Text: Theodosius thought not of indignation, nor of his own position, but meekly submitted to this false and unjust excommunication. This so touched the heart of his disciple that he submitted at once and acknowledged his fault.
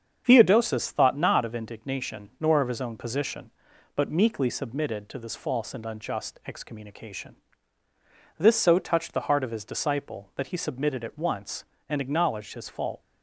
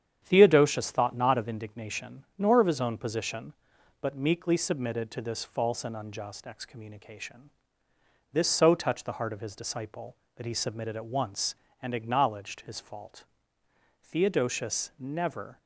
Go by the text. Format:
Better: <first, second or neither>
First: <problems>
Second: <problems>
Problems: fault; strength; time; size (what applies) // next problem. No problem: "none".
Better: first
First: starts louder than the rest; strong; until 1.2 s; 7.5 dB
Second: starts louder than the rest; strong; until 1.2 s; 8.5 dB // goes on to say "Theodosius never"; from 14.0 s on; 1.5 s long